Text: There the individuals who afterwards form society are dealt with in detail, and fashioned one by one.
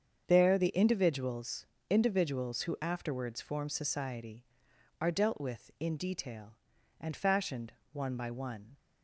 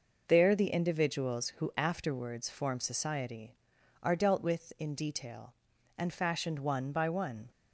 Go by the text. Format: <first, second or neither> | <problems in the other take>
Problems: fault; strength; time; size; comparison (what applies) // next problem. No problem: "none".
second | starts louder than the rest; strong; until 1.2 s; 7.5 dB // says "individuals" twice; at 1.8 s // pauses between "fashioned" and "one"; slight; at 7.7 s; 0.18 s long